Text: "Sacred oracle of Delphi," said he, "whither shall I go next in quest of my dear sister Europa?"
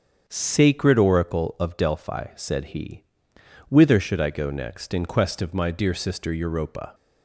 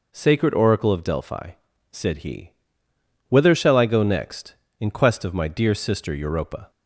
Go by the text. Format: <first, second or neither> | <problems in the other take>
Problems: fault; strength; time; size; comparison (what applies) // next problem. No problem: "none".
second | starts louder than the rest; strong; until 1.2 s; 7.5 dB // says "should" for "shall"; at 4.0 s